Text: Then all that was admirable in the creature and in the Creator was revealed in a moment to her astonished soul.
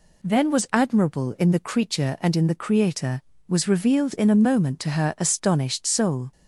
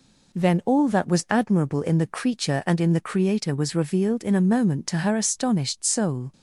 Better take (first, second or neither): second